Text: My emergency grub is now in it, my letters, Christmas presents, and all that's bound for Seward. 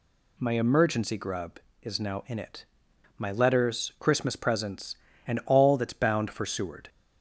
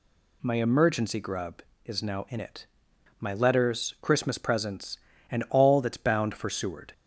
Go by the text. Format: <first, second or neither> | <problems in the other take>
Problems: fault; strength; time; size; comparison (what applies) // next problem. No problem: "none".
neither | none